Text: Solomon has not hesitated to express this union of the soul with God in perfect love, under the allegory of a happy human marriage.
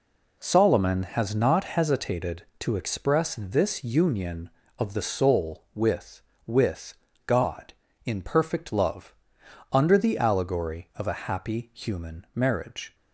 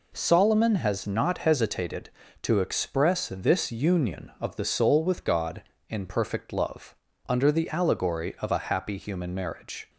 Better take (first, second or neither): second